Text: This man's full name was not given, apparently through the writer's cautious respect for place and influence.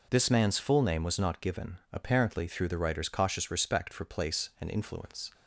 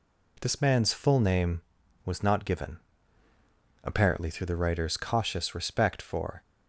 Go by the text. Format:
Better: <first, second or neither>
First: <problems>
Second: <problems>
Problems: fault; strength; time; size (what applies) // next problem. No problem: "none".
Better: first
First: none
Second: stops before "place and influence"; at 6.4 s